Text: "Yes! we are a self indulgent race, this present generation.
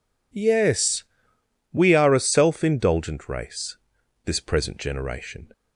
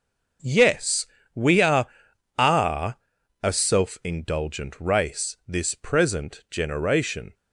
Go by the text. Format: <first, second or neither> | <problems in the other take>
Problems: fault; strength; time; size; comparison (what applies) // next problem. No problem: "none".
first | says "are" twice; at 2.3 s